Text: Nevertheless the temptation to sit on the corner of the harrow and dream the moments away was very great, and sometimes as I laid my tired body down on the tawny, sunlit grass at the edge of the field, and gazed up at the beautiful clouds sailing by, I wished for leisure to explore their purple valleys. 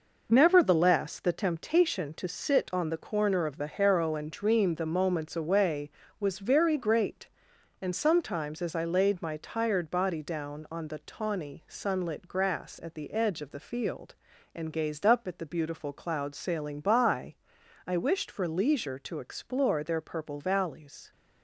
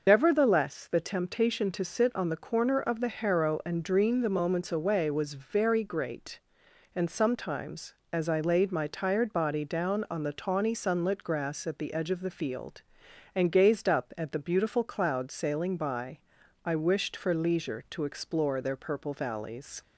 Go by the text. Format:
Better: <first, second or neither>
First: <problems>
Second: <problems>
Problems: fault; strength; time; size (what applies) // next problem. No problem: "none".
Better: first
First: none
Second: loses the start of "Nevertheless"; at 0.0 s; 80 ms // starts louder than the rest; noticeable; until 1.0 s; 6 dB